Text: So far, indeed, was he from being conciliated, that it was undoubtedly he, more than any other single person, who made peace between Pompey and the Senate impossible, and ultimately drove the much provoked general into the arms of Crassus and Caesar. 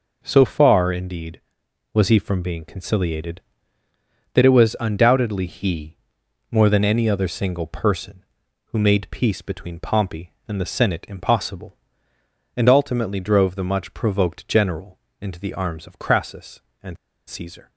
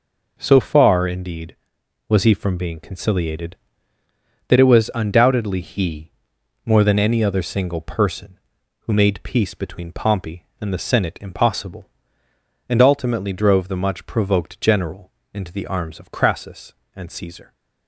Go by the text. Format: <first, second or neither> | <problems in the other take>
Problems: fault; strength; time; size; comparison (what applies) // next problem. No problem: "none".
second | pauses between "general" and "into"; slight; at 14.9 s; 0.20 s long; slight in the second // pauses between "and" and "Caesar"; slight; at 16.9 s; 0.31 s long